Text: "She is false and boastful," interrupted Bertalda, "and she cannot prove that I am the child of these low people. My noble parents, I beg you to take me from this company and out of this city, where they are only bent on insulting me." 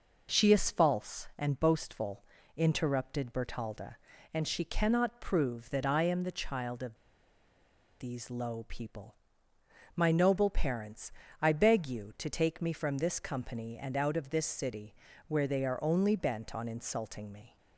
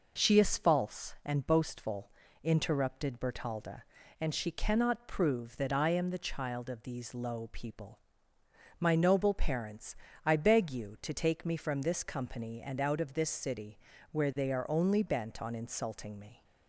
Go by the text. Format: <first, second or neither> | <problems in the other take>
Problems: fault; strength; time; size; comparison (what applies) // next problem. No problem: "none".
second | pauses between "of" and "these"; at 6.9 s; 1.0 s long